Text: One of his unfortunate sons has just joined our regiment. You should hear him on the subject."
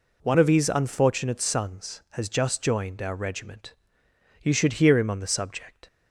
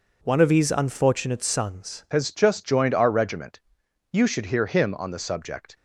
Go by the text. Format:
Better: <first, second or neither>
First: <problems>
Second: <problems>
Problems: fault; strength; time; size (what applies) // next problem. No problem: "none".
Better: first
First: none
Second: changes voice at "has"; from 2.1 s on; 3.6 s long